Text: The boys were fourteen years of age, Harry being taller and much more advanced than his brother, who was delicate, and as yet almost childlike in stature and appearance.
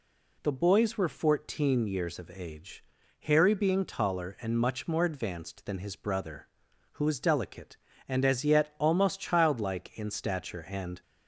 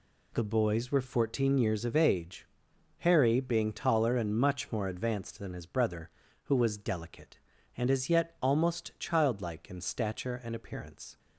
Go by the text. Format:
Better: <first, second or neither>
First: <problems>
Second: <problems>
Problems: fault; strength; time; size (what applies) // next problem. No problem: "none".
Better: second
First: stops before "appearance"; at 11.0 s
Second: none